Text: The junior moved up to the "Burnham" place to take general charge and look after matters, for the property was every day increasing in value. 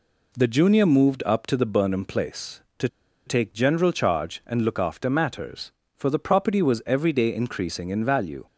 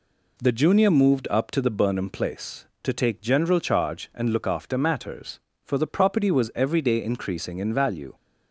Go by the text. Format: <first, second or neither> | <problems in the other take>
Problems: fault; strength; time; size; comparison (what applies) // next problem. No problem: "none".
second | pauses between "to" and "take"; at 2.8 s; 0.38 s long